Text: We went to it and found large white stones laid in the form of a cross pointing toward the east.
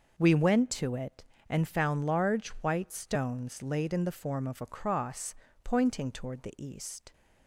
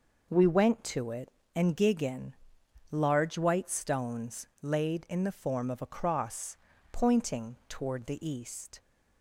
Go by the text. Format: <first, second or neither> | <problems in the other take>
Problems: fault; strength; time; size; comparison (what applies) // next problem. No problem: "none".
first | says "gigan" for "found"; at 1.7 s // pauses between "stones" and "laid"; slight; at 4.4 s; 0.16 s long // pauses between "cross" and "pointing"; slight; at 6.5 s; 0.36 s long; slight in the first